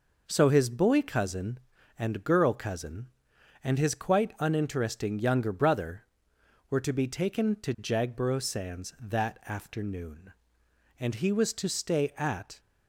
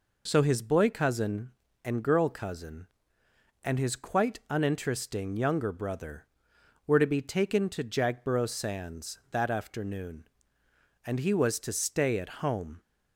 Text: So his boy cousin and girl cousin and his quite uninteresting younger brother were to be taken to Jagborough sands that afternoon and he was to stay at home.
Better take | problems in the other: second | stops before "home"; at 12.5 s

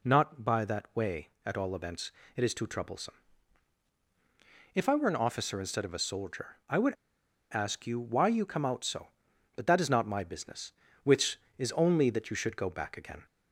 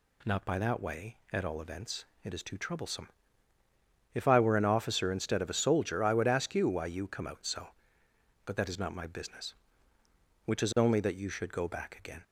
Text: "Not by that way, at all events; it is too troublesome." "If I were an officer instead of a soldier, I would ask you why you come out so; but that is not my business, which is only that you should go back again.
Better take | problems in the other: second | pauses between "would" and "ask"; noticeable; at 6.9 s; 0.56 s long

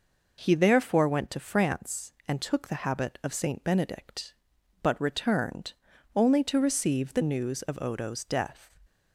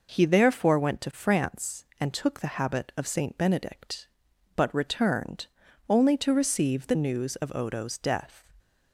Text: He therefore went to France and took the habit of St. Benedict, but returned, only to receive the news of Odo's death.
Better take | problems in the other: neither | none

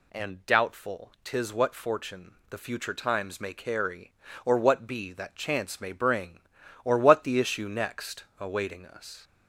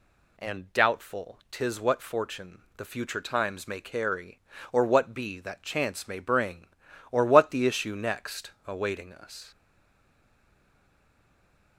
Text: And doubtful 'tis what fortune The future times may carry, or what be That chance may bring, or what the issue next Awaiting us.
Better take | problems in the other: first | pauses between "fortune" and "The"; slight; at 2.6 s; 0.16 s long; slight in the first // pauses between "next" and "Awaiting"; slight; at 8.5 s; 0.16 s long; slight in the first // stays silent after the last word; from 9.5 s on; 2.2 s long

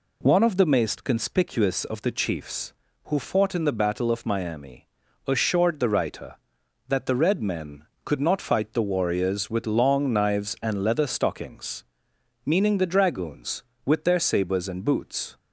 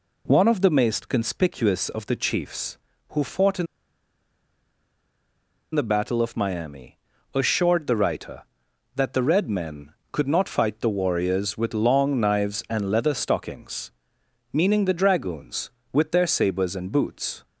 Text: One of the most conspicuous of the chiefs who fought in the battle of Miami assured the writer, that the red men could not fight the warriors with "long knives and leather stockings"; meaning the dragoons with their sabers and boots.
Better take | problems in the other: first | pauses between "in" and "the"; strong; at 3.6 s; 2.0 s long // pauses between "Miami" and "assured"; at 6.9 s; 0.38 s long; also in the first

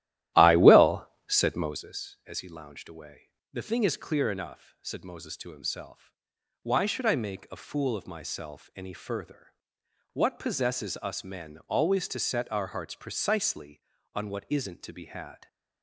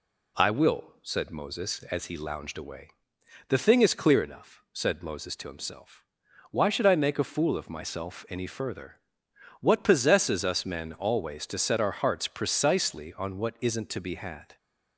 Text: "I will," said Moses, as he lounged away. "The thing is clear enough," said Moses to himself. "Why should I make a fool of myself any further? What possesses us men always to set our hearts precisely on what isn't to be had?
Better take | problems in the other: second | starts louder than the rest; strong; until 1.9 s; 13.5 dB

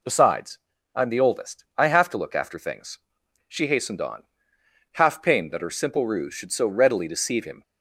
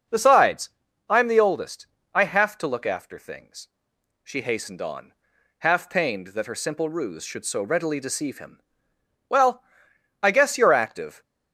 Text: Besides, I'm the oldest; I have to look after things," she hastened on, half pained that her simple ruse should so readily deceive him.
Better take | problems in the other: first | starts louder than the rest; noticeable; until 1.5 s; 6 dB // goes on to say "Well I guess you're active"; strong; from 9.2 s on; 1.9 s long

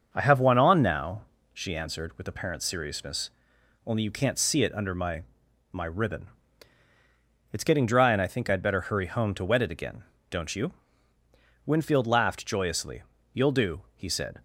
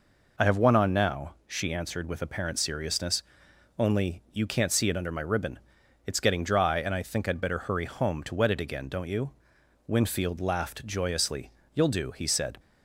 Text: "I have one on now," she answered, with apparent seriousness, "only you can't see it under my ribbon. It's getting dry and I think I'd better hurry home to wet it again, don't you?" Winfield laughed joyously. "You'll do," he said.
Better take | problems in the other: second | starts louder than the rest; until 1.1 s; 6.5 dB // says "my" twice; at 5.7 s

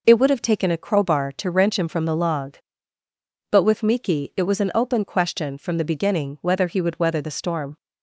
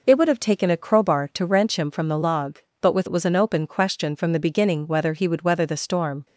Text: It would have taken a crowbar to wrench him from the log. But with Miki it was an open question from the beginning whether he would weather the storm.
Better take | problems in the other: first | skips "Miki"; at 3.0 s

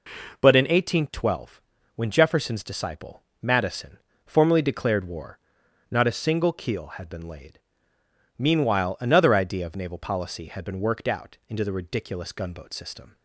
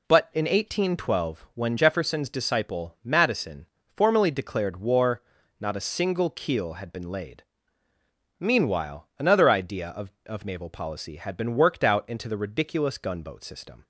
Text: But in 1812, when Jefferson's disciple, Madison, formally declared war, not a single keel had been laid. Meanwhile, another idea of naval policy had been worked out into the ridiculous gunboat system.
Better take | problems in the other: first | says "of" twice; at 10.2 s

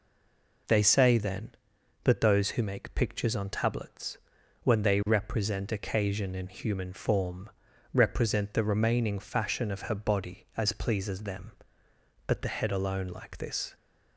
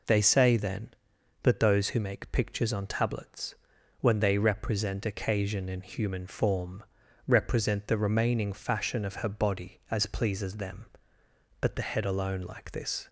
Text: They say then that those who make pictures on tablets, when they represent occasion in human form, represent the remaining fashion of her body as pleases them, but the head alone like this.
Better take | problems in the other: second | stays silent before the first word; slight; until 0.6 s; 0.6 s long

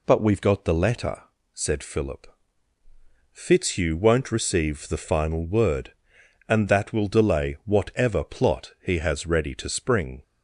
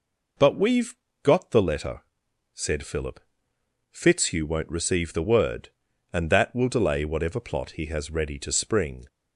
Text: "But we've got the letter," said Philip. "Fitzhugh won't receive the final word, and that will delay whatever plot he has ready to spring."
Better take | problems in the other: first | pauses between "we've" and "got"; slight; at 0.9 s; 0.28 s long // skips "final"; at 5.2 s

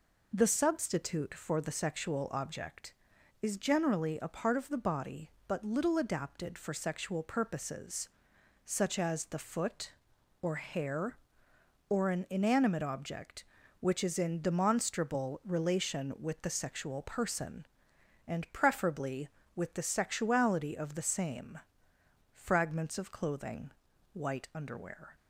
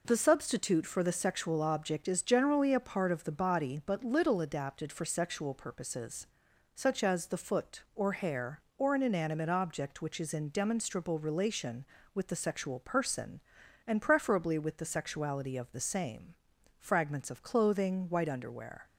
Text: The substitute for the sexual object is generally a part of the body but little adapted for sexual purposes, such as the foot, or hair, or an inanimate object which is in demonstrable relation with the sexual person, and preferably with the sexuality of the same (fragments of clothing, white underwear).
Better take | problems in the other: neither | none

